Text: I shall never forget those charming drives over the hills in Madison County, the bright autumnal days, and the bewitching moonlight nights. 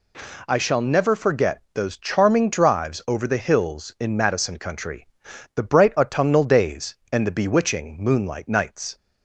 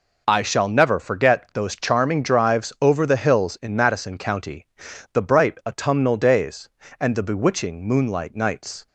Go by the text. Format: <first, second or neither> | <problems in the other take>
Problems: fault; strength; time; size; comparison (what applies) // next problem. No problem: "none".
second | says "Country" for "County"; at 4.5 s